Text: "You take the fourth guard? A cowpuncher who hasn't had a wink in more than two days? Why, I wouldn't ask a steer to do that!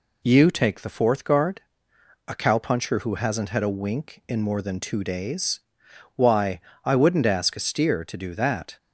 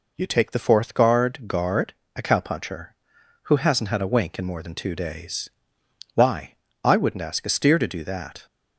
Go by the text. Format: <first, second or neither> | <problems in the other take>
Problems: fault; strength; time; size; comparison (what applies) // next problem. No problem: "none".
first | says "guard" twice; at 1.4 s